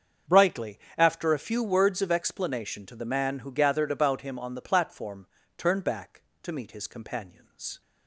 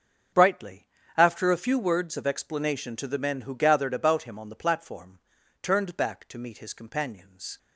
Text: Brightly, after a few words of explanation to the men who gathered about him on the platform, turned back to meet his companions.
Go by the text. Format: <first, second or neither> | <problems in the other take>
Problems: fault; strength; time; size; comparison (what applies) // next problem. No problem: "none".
second | starts louder than the rest; until 1.4 s; 7 dB; also in the second // says "man" for "men"; at 3.0 s